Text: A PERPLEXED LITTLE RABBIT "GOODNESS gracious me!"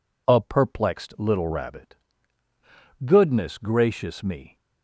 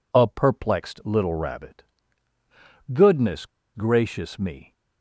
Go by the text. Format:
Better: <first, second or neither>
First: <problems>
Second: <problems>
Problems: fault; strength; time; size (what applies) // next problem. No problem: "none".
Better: first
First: pauses between "RABBIT" and "GOODNESS"; at 1.9 s; 1.0 s long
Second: pauses between "RABBIT" and "GOODNESS"; at 1.8 s; 1.0 s long // pauses between "GOODNESS" and "gracious"; slight; at 3.4 s; 0.29 s long